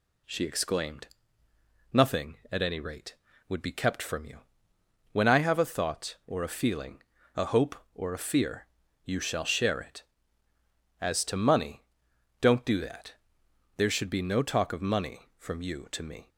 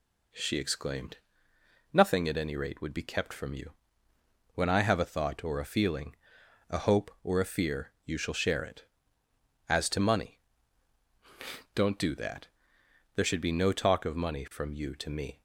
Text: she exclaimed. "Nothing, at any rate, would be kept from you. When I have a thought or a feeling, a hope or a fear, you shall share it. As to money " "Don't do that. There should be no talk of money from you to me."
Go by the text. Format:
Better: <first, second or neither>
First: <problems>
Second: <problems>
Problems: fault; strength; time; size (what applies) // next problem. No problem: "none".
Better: neither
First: none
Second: none